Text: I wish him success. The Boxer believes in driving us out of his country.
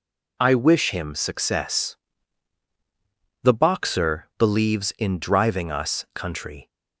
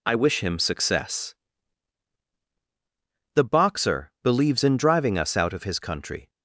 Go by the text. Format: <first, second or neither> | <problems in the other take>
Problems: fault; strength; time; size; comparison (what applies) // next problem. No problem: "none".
second | skips "out of his"; at 6.0 s